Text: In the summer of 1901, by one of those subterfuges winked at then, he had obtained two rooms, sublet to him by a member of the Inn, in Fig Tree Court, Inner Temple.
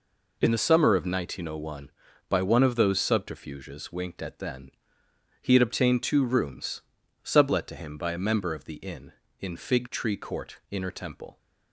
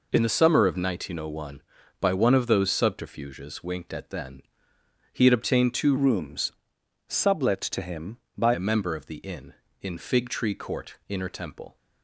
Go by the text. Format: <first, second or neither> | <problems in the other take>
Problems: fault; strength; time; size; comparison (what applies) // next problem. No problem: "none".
first | changes voice from "rooms" to "by"; from 5.9 to 8.5 s; 2.6 s long